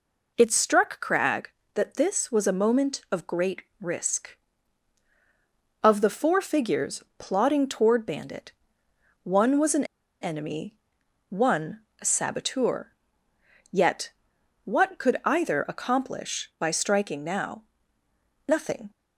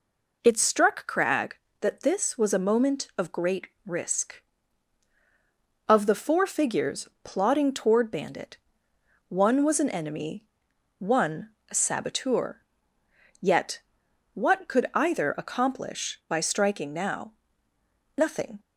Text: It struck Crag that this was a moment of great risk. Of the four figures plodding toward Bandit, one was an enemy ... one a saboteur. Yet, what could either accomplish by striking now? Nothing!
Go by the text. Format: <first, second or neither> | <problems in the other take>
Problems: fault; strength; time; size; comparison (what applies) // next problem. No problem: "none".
second | pauses between "great" and "risk"; slight; at 3.6 s; 0.18 s long; slight in the second // pauses between "figures" and "plodding"; slight; at 7.0 s; 0.16 s long; slight in the second // pauses between "an" and "enemy"; at 9.8 s; 0.37 s long // pauses between "one" and "a"; slight; at 11.8 s; 0.20 s long; slight in the second